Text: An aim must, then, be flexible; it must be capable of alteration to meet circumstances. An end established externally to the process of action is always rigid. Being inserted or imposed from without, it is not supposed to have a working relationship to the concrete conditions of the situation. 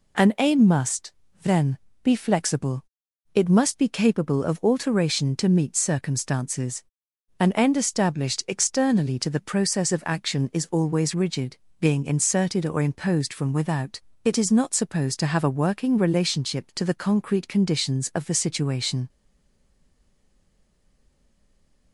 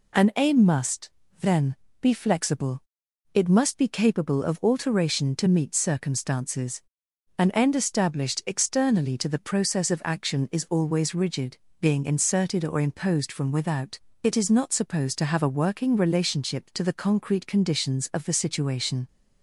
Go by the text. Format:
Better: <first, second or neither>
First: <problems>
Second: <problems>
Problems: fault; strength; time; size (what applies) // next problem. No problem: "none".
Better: second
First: stays silent after the last word; strong; from 19.0 s on; 2.9 s long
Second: none